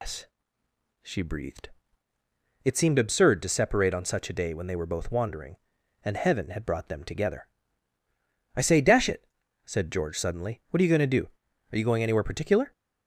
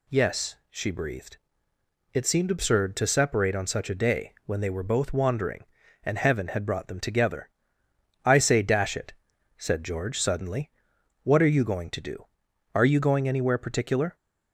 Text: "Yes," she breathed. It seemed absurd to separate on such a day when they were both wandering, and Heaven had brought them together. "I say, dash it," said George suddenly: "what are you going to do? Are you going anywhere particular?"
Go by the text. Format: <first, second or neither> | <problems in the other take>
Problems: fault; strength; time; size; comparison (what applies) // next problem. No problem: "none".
second | loses the start of "Yes"; at 0.0 s; 175 ms